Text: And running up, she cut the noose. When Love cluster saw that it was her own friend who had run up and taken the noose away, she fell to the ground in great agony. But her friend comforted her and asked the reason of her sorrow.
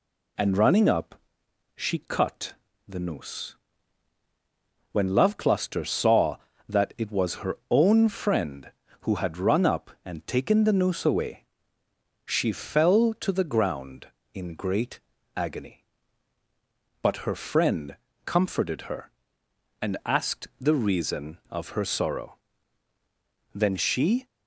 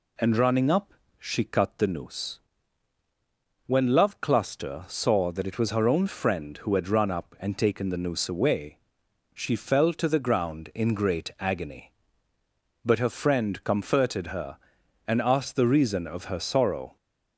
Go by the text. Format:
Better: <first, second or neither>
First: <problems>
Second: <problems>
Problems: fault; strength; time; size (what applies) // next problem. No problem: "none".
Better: second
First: pauses between "cut" and "the"; slight; at 2.5 s; 0.34 s long // pauses between "great" and "agony"; slight; at 14.9 s; 0.36 s long // pauses between "friend" and "comforted"; slight; at 17.9 s; 0.30 s long // goes on to say "Then she"; noticeable; from 23.5 s on; 0.72 s long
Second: none